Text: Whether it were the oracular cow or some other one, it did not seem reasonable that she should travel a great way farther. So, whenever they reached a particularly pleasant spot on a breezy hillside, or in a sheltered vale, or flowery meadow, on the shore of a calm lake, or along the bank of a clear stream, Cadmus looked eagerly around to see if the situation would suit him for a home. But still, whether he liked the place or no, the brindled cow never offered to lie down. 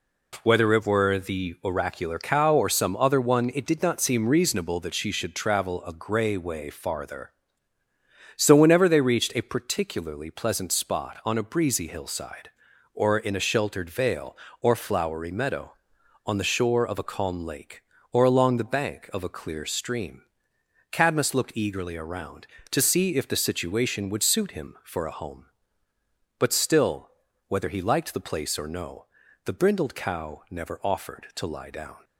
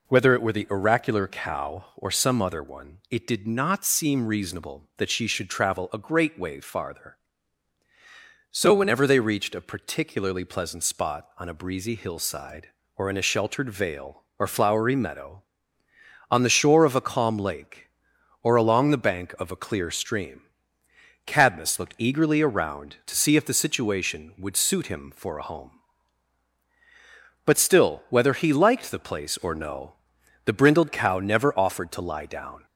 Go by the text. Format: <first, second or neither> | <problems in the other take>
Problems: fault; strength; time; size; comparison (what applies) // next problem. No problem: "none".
second | says "grey" for "great"; at 5.9 s